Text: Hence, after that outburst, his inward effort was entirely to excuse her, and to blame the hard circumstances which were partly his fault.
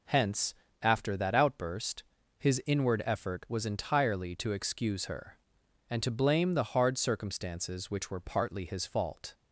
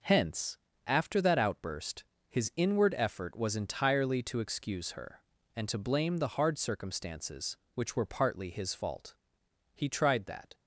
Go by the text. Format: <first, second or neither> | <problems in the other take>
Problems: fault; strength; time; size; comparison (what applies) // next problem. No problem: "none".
first | goes on to say "He tried that"; noticeable; from 9.7 s on; 0.80 s long